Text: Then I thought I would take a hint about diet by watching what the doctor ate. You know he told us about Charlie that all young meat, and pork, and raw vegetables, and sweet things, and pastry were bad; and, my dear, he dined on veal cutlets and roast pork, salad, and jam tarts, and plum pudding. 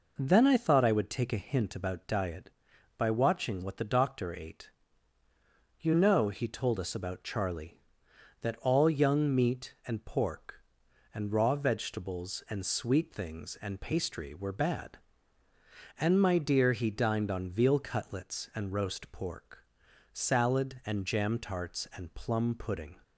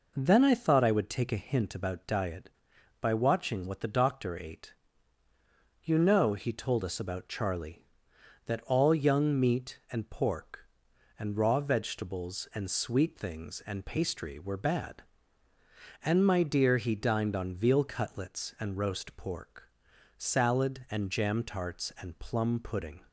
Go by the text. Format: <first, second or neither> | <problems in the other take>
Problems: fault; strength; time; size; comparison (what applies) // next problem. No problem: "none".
neither | none